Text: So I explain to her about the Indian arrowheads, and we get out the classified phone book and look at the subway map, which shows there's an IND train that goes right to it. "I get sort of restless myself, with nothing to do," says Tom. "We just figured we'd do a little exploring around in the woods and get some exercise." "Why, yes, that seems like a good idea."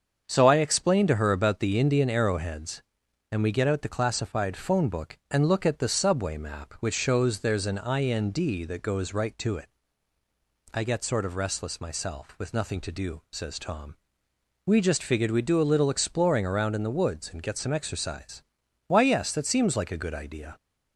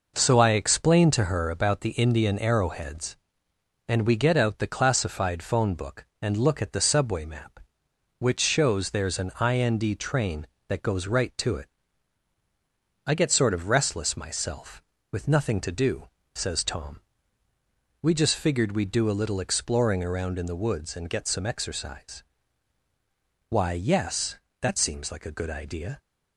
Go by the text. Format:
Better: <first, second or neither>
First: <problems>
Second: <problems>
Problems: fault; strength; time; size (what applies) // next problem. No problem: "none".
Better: second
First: starts louder than the rest; until 1.2 s; 7 dB // skips "train"; at 8.6 s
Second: none